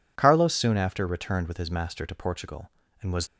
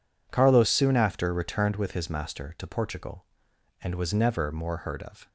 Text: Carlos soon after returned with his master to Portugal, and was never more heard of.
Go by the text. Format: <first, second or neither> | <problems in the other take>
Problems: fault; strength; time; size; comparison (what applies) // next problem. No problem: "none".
second | stops before "never more heard of"; at 3.2 s